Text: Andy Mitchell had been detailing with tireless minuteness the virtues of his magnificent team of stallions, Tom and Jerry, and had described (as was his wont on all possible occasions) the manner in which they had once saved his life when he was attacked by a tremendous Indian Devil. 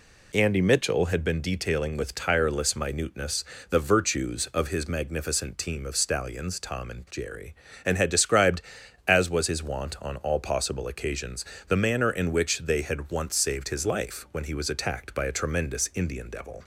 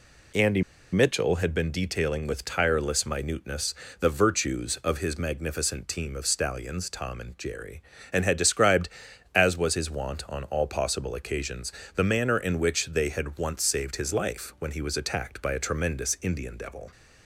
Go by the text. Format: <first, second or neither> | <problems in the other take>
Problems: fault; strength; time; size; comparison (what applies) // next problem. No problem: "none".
first | pauses between "Andy" and "Mitchell"; slight; at 0.6 s; 0.30 s long // pauses between "minuteness" and "the"; slight; at 3.7 s; 0.28 s long; slight in the first